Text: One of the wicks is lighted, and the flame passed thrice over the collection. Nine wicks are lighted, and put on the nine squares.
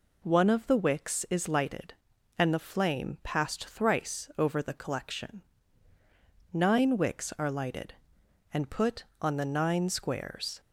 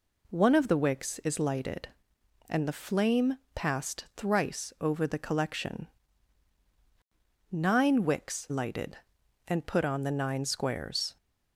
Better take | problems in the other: first | pauses between "flame" and "passed"; slight; at 3.3 s; 0.16 s long // skips "are"; at 8.4 s

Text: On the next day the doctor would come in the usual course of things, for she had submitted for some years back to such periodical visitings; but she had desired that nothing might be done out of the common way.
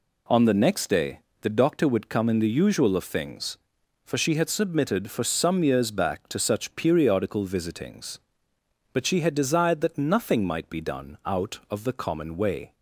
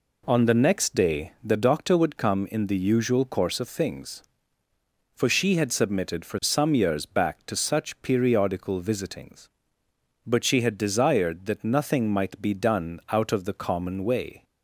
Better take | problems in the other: second | pauses between "day" and "the"; slight; at 1.1 s; 0.22 s long // skips "course"; at 2.9 s

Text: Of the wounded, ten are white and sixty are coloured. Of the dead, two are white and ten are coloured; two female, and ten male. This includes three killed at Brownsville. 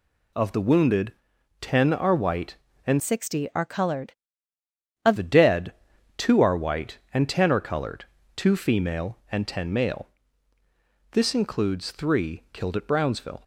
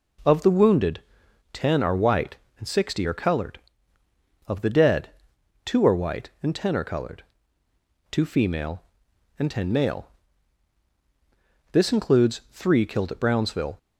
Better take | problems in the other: second | changes voice from "sixty" to "Of"; from 3.0 to 5.1 s; 2.1 s long

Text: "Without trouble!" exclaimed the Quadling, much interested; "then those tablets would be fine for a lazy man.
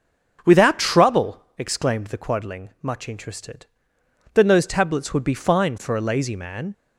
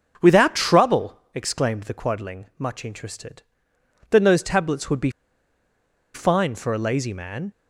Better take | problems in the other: first | starts louder than the rest; until 1.3 s; 6.5 dB; also in the first // pauses between "be" and "fine"; at 5.0 s; 1.0 s long

